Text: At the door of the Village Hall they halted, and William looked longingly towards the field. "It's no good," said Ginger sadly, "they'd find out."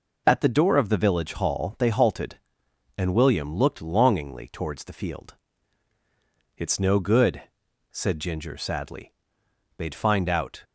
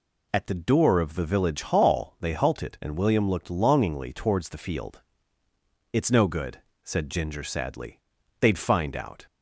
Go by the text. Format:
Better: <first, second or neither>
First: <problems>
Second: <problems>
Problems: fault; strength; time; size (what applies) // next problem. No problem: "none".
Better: neither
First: none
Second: none